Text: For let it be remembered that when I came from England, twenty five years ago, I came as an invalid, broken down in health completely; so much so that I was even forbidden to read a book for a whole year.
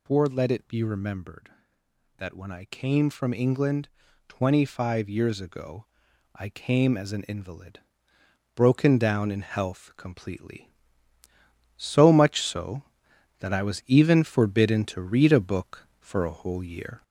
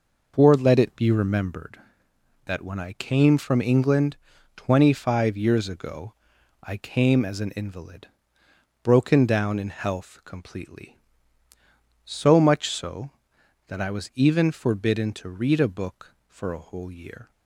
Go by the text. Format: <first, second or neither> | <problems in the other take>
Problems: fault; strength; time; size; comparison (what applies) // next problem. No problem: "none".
second | gets louder; slight; throughout; 2 dB